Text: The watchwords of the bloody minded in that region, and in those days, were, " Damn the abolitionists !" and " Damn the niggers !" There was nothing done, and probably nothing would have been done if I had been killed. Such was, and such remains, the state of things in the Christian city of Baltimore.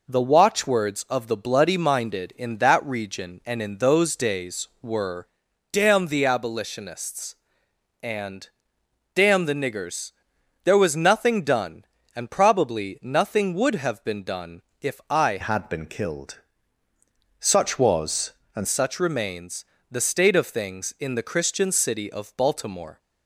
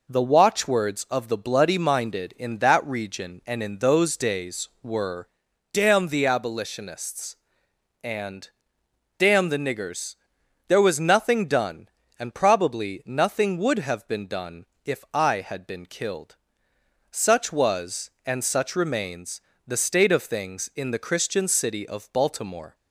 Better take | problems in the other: second | pauses between "done" and "if"; slight; at 14.6 s; 0.18 s long; slight in the second // changes voice from "had" to "and"; from 15.4 to 18.6 s; 3.2 s long

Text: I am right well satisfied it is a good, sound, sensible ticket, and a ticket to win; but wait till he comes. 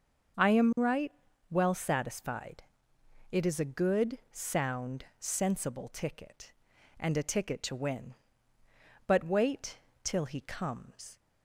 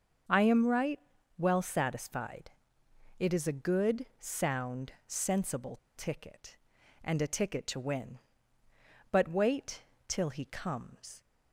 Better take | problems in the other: first | starts louder than the rest; until 1.6 s; 6.5 dB; also in the first // pauses between "right" and "well"; at 0.9 s; 0.40 s long; also in the first // pauses between "satisfied" and "it"; noticeable; at 2.5 s; 0.68 s long; noticeable in the first // pauses between "sensible" and "ticket"; slight; at 5.7 s; 0.18 s long // pauses between "wait" and "till"; slight; at 9.8 s; 0.26 s long; slight in the first

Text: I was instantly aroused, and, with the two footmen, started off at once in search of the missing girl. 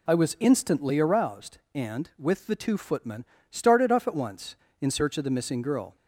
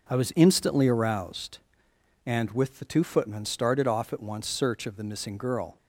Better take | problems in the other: first | skips "in"; at 4.4 s

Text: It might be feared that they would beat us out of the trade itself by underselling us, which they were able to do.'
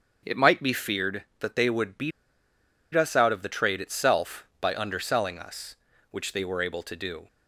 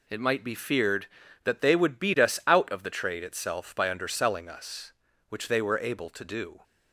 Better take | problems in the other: second | starts louder than the rest; until 1.2 s; 7 dB // pauses between "beat" and "us"; noticeable; at 2.1 s; 0.84 s long

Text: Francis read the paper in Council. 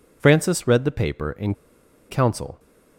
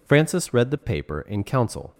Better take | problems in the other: second | pauses between "in" and "Council"; noticeable; at 1.5 s; 0.54 s long

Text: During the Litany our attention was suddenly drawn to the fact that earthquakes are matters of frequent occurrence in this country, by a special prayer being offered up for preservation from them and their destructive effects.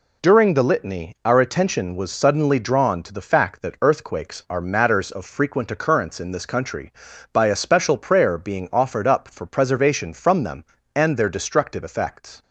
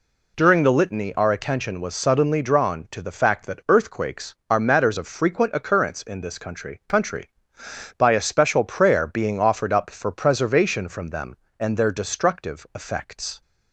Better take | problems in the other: first | says "country" twice; at 6.8 s

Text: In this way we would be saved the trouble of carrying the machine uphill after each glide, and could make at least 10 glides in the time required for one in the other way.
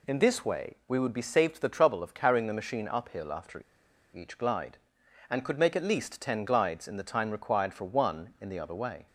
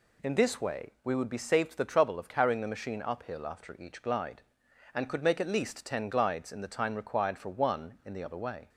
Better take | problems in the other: second | pauses between "after" and "each"; noticeable; at 3.6 s; 0.51 s long

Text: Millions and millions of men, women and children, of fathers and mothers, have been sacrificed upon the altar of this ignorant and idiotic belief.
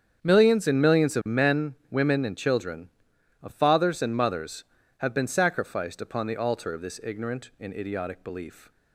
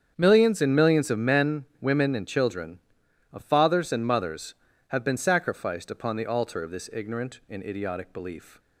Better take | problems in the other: neither | starts louder than the rest; strong; the same in both

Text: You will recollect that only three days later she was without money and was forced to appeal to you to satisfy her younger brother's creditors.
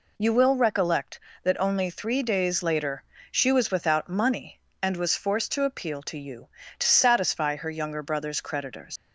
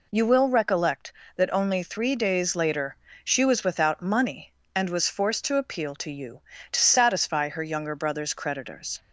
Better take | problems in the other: second | pauses between "later" and "she"; slight; at 3.0 s; 0.28 s long; slight in the second // leaves "creditors" unfinished; at 8.9 s; 115 ms

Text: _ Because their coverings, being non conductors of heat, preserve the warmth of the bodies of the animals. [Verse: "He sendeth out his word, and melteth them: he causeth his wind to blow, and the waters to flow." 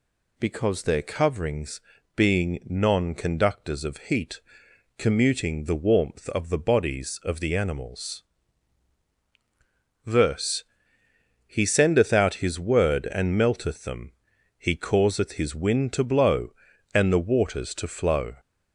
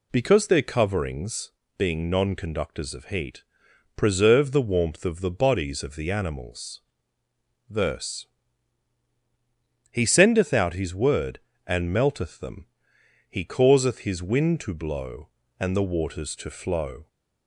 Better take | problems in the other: second | says "commuting" for "preserve"; at 4.9 s

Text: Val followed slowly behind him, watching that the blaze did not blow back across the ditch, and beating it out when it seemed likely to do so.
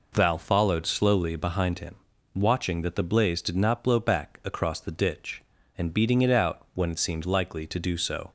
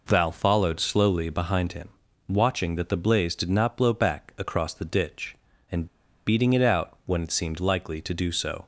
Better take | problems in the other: first | pauses between "and" and "beating"; at 5.8 s; 0.40 s long

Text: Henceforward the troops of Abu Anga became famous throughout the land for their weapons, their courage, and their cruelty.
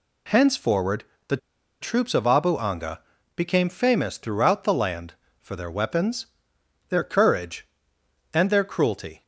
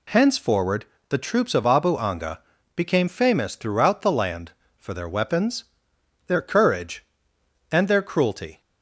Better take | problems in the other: second | pauses between "Henceforward" and "the"; slight; at 1.0 s; 0.24 s long; slight in the second // pauses between "the" and "troops"; at 1.3 s; 0.44 s long // pauses between "Anga" and "became"; slight; at 3.0 s; 0.36 s long; slight in the second

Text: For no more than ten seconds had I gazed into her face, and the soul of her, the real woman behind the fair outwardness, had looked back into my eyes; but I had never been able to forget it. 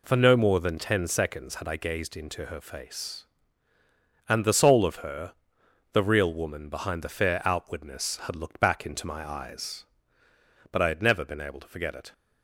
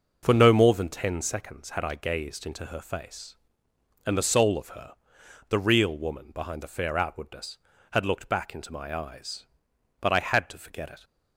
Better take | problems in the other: first | skips "never been able"; at 10.4 s

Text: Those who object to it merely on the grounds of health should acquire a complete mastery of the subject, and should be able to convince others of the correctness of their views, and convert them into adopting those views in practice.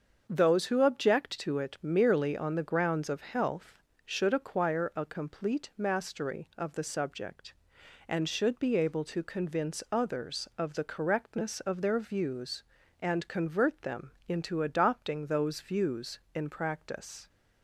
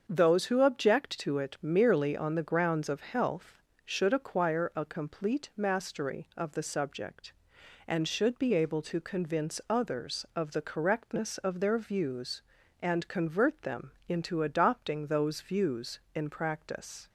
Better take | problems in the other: neither | starts louder than the rest; the same in both

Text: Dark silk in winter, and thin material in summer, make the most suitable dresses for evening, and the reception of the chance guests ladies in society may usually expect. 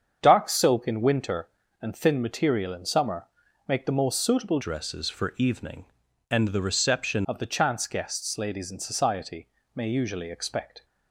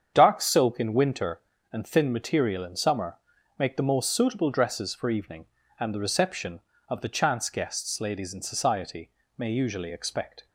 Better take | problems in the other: second | starts louder than the rest; strong; until 1.2 s; 7.5 dB; strong in the second // changes voice from "dresses" to "reception"; from 4.5 to 7.2 s; 2.7 s long // pauses between "society" and "may"; slight; at 9.4 s; 0.26 s long; slight in the second

